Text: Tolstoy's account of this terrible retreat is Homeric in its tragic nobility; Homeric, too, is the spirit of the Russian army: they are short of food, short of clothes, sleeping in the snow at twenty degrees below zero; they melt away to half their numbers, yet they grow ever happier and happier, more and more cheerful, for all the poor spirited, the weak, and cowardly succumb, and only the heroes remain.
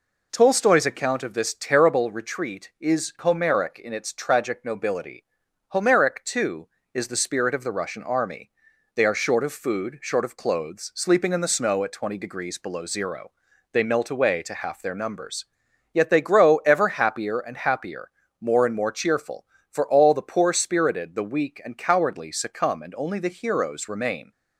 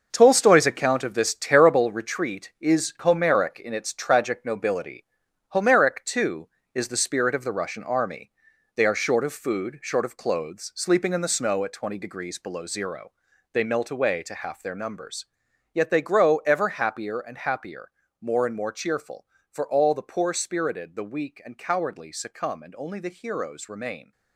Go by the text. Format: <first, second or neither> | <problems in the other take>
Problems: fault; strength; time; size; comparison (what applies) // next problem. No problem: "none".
first | gets quieter; strong; throughout; 10 dB